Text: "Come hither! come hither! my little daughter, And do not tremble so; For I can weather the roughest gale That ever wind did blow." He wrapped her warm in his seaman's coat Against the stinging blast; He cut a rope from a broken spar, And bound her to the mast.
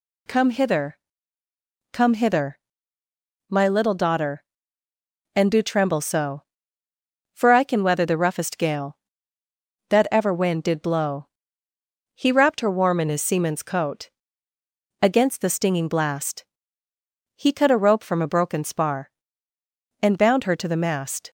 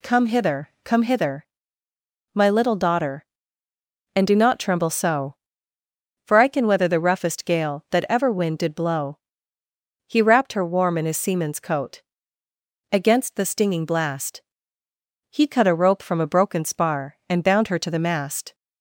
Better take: second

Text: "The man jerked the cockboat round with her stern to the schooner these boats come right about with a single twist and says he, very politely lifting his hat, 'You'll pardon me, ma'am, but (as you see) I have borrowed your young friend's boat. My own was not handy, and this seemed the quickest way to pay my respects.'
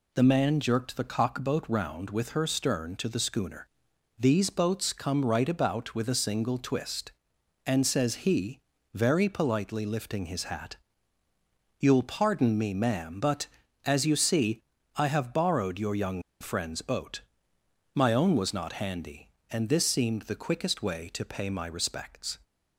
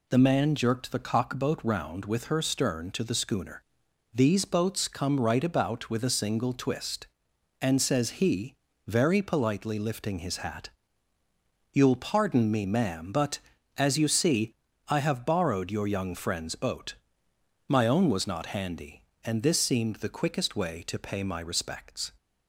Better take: second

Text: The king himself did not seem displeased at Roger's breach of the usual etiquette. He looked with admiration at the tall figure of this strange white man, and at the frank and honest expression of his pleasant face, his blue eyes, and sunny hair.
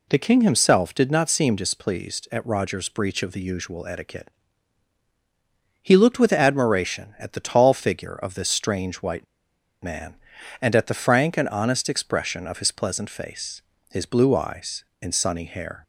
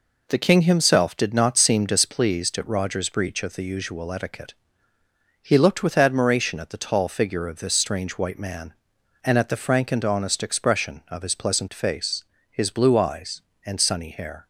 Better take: second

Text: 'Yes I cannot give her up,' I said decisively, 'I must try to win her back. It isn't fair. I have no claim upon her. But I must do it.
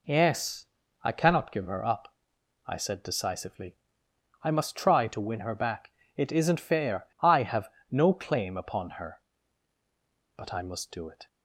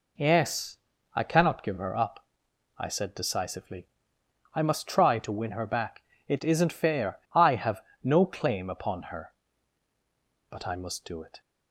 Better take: neither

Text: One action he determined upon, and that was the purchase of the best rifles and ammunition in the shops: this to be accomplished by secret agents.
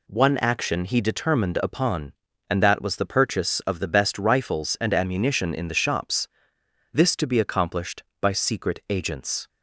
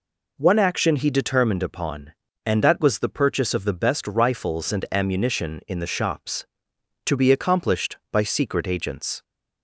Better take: first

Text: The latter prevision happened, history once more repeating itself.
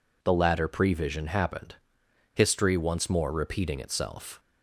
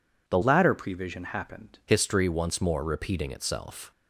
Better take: first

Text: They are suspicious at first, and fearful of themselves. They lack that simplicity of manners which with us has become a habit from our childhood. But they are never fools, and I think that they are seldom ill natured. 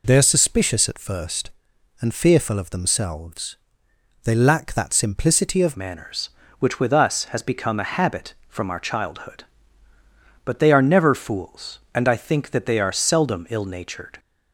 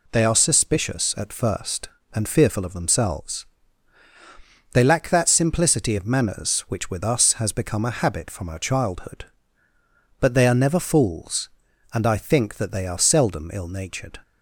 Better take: second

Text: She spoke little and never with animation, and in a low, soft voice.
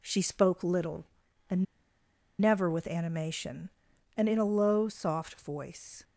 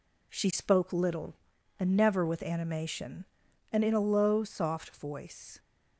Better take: second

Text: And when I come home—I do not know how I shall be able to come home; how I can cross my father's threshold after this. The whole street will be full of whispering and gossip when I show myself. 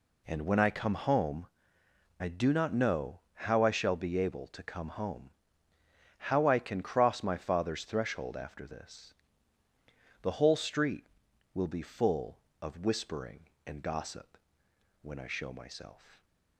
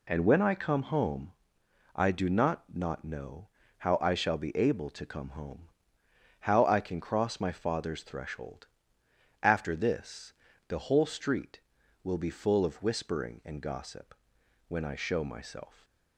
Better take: first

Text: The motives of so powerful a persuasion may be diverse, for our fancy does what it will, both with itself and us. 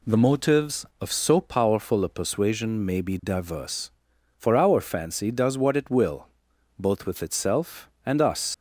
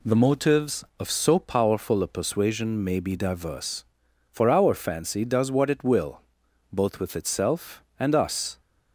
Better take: second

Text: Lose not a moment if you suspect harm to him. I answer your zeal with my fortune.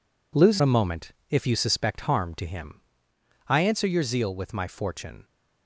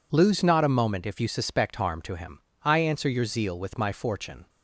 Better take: second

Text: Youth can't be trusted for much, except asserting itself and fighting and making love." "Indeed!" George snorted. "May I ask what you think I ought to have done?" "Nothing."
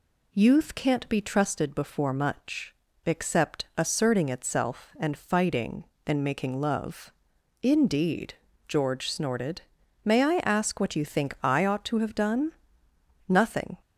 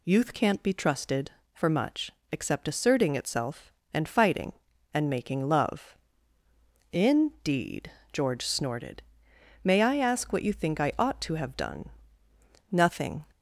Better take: second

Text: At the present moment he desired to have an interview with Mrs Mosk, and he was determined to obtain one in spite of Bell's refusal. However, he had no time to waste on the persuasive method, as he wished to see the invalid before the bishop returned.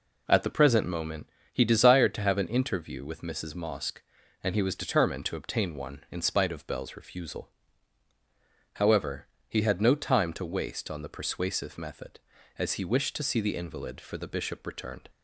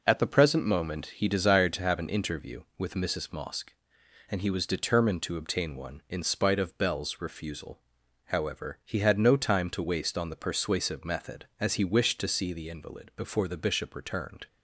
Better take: second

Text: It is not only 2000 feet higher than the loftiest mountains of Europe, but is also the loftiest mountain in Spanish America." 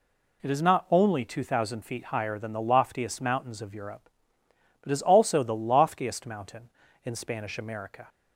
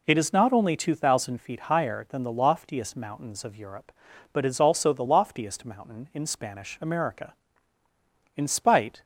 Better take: first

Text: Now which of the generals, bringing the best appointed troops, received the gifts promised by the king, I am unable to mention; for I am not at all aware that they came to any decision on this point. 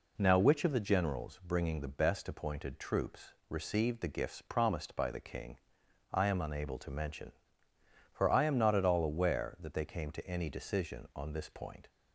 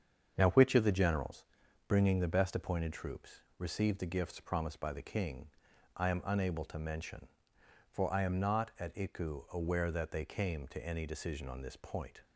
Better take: first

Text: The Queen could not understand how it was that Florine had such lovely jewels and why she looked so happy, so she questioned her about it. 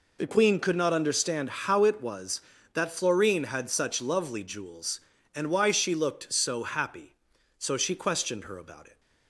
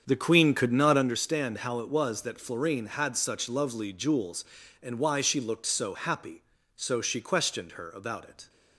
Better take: first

